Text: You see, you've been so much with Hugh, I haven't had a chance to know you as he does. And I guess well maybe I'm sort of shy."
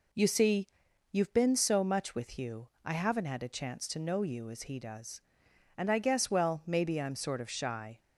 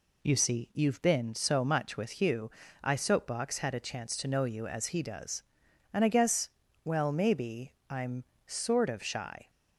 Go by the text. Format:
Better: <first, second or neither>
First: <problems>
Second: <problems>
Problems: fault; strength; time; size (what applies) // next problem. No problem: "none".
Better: first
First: none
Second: says "soapbox" for "haven't"; at 2.9 s // pauses between "guess" and "well"; slight; at 6.4 s; 0.34 s long // pauses between "maybe" and "I'm"; slight; at 7.7 s; 0.18 s long // pauses between "I'm" and "sort"; slight; at 8.2 s; 0.22 s long